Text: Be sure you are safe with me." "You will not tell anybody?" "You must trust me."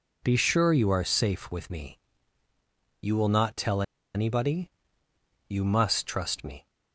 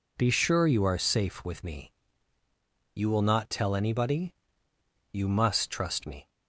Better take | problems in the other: second | pauses between "tell" and "anybody"; slight; at 3.8 s; 0.32 s long

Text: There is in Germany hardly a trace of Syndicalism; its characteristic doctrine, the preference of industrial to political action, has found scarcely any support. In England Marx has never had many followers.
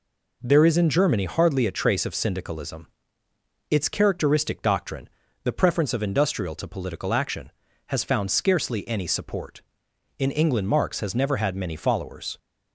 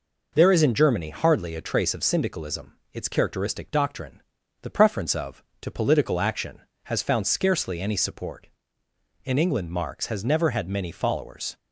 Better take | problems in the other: first | skips "industrial"; at 5.5 s

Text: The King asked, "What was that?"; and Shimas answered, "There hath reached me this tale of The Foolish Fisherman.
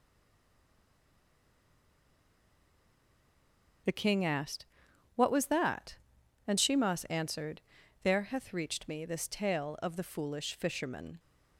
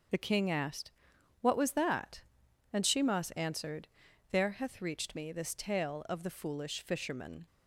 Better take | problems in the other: second | stays silent before the first word; strong; until 3.8 s; 3.8 s long // starts louder than the rest; until 5.3 s; 6.5 dB; also in the second

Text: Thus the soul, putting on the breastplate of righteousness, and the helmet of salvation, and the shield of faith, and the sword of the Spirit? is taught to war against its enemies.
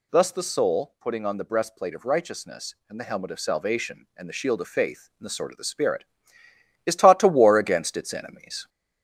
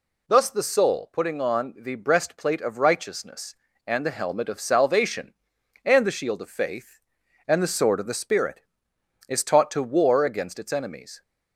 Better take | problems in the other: second | gets louder; slight; throughout; 2.5 dB

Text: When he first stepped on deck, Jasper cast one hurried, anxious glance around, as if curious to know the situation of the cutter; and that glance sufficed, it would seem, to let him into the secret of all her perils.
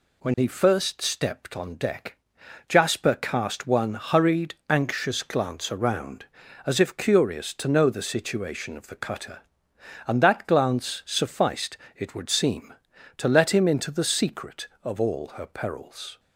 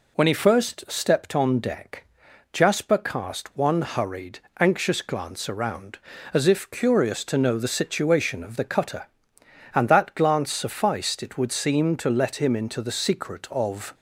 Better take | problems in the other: first | stops before "all her perils"; at 13.9 s

